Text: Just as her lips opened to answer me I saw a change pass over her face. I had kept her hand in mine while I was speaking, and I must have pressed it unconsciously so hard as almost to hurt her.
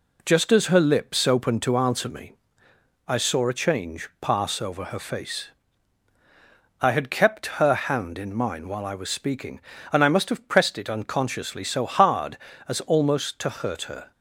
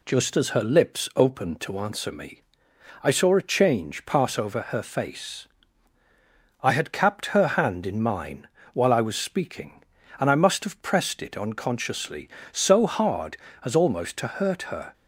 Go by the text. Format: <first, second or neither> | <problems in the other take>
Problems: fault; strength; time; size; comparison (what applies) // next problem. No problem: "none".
first | pauses between "me" and "I"; noticeable; at 2.4 s; 0.62 s long; noticeable in the first // says "capped" for "kept"; at 6.9 s // pauses between "mine" and "while"; slight; at 8.4 s; 0.28 s long